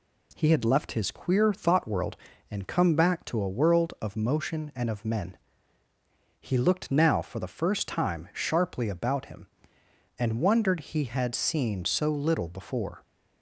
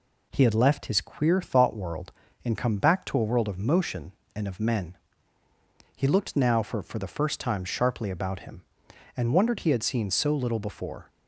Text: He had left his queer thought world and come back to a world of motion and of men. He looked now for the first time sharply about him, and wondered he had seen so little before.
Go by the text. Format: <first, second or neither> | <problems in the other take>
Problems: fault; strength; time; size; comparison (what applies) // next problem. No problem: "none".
first | says "for" twice; at 6.8 s